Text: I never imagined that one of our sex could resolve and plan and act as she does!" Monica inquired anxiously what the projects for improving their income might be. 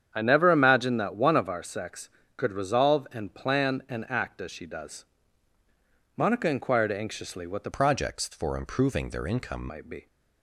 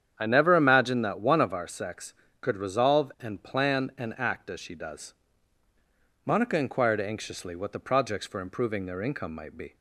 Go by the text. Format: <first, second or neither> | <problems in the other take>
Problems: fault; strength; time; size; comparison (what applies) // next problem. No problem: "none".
second | starts louder than the rest; strong; until 1.1 s; 8 dB; strong in the second // changes voice from "projects" to "income"; from 7.7 to 9.6 s; 1.9 s long